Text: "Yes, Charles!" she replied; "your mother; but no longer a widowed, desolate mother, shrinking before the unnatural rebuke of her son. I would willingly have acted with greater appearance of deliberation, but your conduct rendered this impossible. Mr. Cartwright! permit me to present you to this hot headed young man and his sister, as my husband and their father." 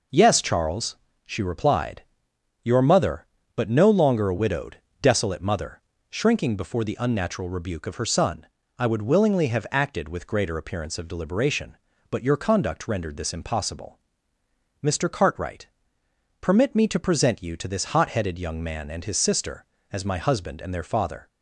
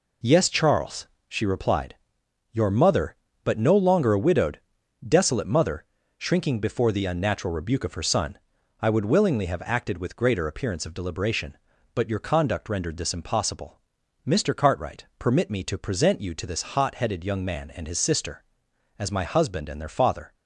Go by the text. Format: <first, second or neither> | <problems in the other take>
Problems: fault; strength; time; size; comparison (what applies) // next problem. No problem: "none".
neither | none